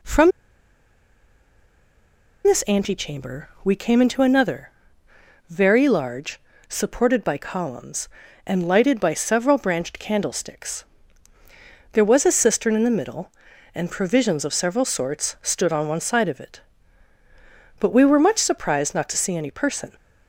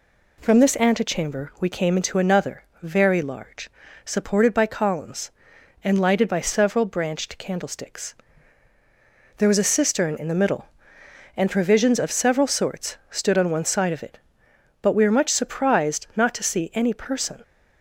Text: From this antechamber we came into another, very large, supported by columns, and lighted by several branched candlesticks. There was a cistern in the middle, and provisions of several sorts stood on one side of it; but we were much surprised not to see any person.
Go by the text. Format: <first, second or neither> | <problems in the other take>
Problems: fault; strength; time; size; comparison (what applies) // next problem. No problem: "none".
second | pauses between "From" and "this"; strong; at 0.3 s; 2.1 s long